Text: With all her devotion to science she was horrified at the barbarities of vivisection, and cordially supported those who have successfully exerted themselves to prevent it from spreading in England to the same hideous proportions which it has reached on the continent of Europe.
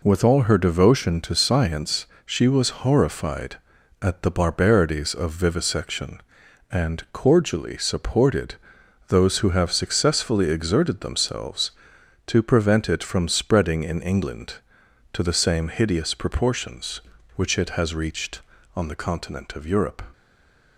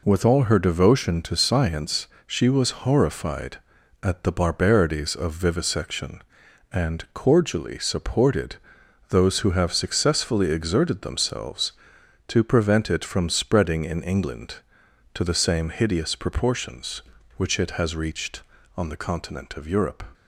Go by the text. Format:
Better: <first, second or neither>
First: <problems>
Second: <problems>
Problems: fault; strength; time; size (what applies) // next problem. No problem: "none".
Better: second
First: pauses between "science" and "she"; slight; at 2.0 s; 0.18 s long // pauses between "supported" and "those"; noticeable; at 8.5 s; 0.52 s long // stays silent after the last word; slight; from 20.1 s on; 0.6 s long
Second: pauses between "science" and "she"; slight; at 2.0 s; 0.18 s long // pauses between "supported" and "those"; noticeable; at 8.5 s; 0.52 s long